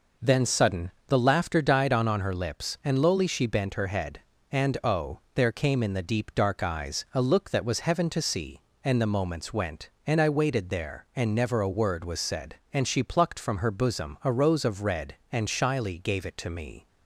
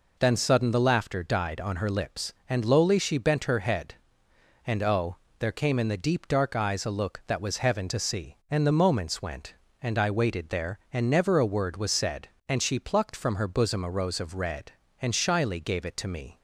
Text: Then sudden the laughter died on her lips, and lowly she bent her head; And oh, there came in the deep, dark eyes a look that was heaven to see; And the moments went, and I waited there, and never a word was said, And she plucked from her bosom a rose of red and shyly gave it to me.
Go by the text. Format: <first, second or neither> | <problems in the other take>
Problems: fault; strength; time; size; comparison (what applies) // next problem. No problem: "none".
second | pauses between "sudden" and "the"; slight; at 0.9 s; 0.18 s long // says "on" twice; at 2.0 s